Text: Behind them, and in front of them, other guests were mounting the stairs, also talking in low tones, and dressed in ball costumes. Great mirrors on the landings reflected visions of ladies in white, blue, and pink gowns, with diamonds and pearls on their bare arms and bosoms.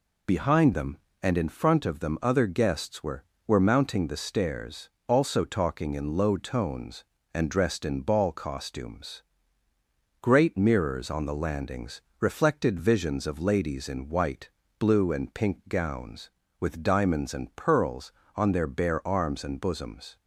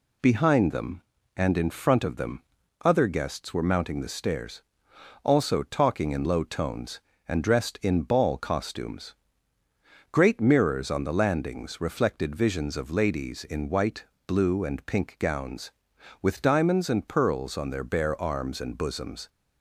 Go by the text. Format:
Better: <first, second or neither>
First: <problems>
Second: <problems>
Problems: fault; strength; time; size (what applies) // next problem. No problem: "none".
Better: second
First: says "were" twice; at 3.4 s // pauses between "landings" and "reflected"; slight; at 12.0 s; 0.20 s long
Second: none